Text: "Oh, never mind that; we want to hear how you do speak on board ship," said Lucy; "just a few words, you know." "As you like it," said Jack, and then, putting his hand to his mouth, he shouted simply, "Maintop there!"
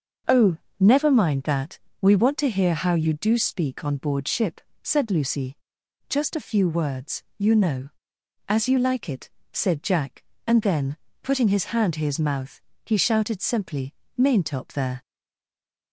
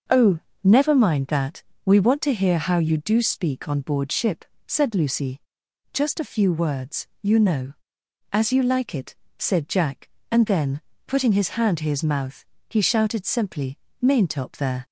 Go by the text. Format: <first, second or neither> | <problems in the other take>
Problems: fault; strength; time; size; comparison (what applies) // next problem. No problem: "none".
second | starts louder than the rest; until 1.5 s; 6 dB; also in the second // stays silent after the last word; slight; from 15.0 s on; 0.9 s long